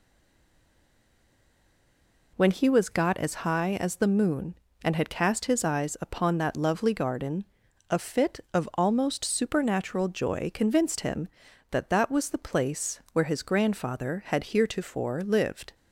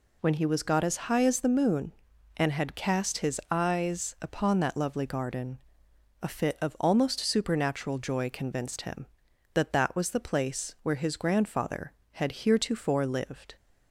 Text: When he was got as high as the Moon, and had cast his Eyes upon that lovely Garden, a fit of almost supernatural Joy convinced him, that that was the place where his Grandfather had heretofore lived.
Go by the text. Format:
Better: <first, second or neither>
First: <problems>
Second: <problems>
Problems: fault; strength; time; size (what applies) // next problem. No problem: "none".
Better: second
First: stays silent before the first word; until 2.3 s; 2.3 s long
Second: none